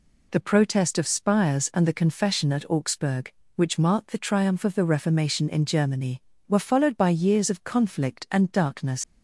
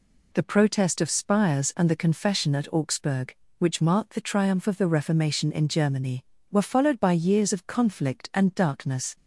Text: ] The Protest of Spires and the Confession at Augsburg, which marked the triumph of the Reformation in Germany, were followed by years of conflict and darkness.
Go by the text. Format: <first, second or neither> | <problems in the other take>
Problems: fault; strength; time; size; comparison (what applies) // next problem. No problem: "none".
second | leaves "darkness" unfinished; at 9.0 s; 90 ms